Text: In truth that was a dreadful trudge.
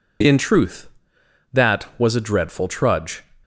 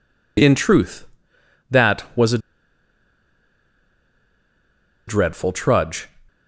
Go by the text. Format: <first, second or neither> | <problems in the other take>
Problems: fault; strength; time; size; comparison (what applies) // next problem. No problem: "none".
first | pauses between "a" and "dreadful"; strong; at 2.3 s; 2.6 s long